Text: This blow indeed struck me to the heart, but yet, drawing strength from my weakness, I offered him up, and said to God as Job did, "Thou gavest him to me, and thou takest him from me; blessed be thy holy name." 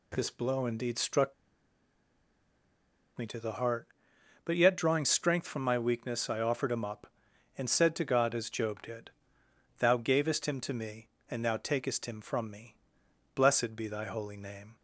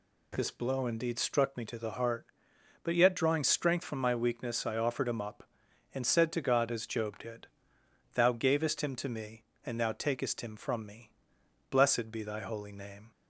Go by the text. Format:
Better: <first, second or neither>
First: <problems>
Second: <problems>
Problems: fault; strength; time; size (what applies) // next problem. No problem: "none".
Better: second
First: pauses between "struck" and "me"; strong; at 1.3 s; 1.8 s long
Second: none